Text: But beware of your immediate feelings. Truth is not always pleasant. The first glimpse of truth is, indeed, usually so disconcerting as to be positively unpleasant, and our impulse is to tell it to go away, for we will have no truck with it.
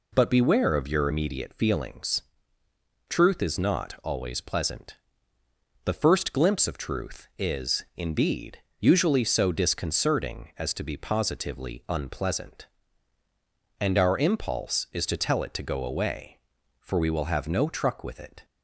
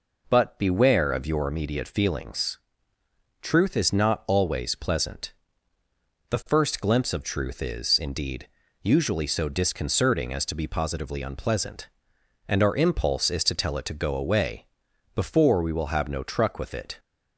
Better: first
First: none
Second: says "before" for "for"; at 15.1 s

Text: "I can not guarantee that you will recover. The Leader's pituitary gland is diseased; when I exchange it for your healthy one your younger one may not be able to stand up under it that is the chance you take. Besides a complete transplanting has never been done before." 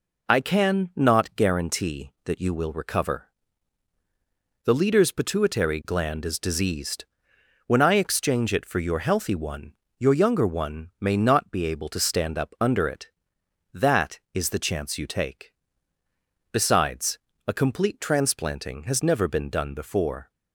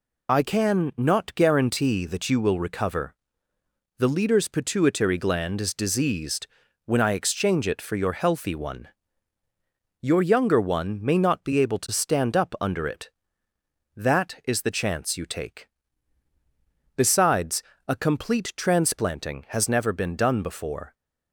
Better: first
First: pauses between "one" and "your"; slight; at 9.7 s; 0.24 s long // pauses between "Besides" and "a"; slight; at 17.1 s; 0.28 s long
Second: loses the start of "I"; at 0.2 s; 25 ms // pauses between "one" and "your"; at 8.8 s; 1.1 s long // pauses between "Besides" and "a"; slight; at 17.6 s; 0.24 s long

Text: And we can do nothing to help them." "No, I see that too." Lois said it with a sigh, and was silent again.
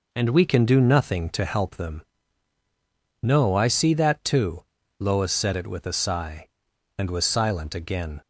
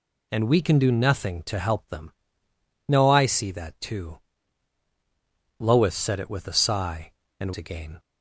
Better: first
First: none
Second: skips "was silent"; at 7.5 s

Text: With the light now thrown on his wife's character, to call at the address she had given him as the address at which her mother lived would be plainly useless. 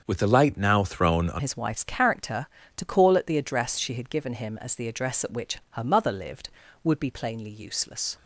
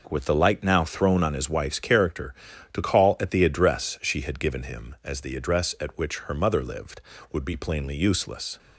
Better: second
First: starts louder than the rest; until 1.0 s; 7 dB // changes voice at "his"; from 1.3 s on; 6.8 s long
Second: none

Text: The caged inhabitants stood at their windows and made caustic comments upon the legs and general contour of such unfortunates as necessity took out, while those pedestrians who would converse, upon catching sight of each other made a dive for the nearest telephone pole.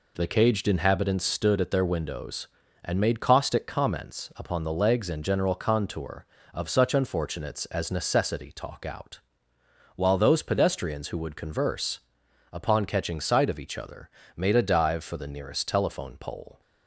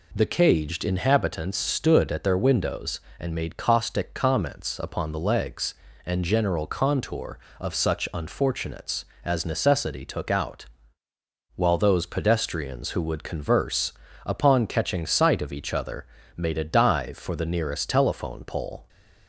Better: second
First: says "talk" for "took"; at 8.5 s // pauses between "other" and "made"; slight; at 14.0 s; 0.30 s long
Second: pauses between "other" and "made"; slight; at 16.0 s; 0.32 s long

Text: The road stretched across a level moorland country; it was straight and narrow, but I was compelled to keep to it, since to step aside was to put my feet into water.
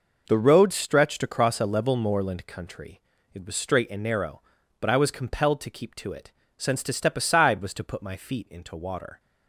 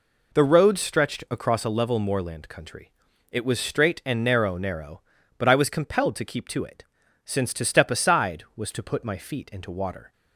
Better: first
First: none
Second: says "narrow" twice; at 4.5 s

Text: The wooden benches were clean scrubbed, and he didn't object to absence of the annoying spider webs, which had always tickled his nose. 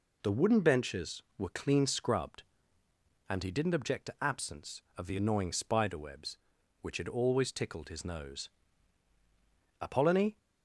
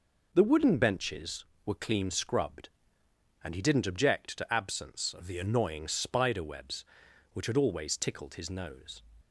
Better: second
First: goes on to say "Apollonie"; from 9.7 s on; 0.58 s long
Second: none

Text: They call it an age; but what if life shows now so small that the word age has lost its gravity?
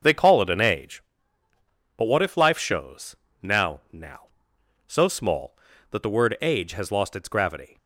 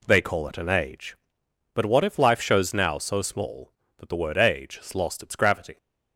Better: second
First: starts louder than the rest; until 1.9 s; 6 dB // pauses between "shows" and "now"; slight; at 3.1 s; 0.26 s long // says "now" twice; at 3.9 s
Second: none

